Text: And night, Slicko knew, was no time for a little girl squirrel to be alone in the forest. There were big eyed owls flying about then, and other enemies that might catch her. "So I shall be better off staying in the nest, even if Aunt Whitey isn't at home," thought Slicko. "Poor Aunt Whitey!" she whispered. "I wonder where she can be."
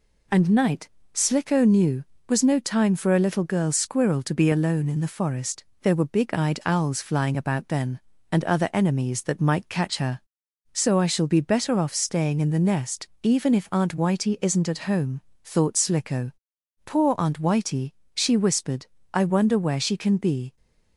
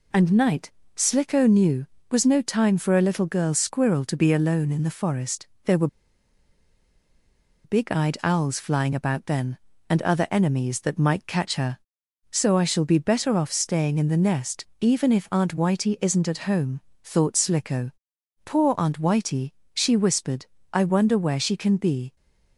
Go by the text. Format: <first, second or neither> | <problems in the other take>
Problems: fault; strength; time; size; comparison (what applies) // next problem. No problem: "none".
first | pauses between "were" and "big"; strong; at 5.8 s; 1.7 s long